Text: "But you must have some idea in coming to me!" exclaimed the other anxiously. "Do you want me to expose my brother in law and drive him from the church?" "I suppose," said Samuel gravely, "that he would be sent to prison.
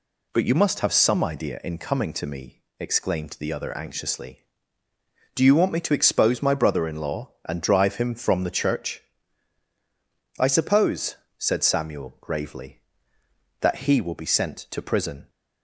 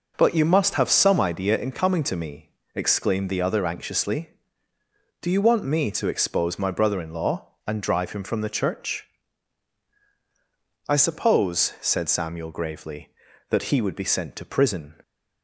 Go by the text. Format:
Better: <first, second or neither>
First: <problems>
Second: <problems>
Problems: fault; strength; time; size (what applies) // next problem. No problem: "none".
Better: second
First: says "will" for "would"; at 13.9 s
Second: none